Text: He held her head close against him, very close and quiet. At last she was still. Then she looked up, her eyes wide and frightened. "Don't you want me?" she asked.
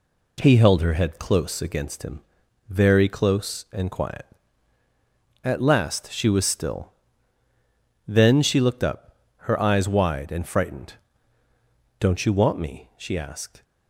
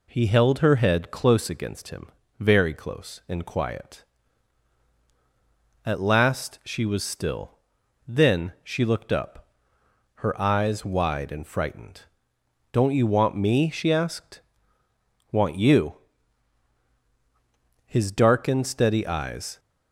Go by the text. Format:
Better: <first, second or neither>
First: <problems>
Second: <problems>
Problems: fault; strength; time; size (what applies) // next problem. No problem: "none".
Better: first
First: none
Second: goes on to say "Want you His darkened steady eyes"; strong; from 15.3 s on; 4.2 s long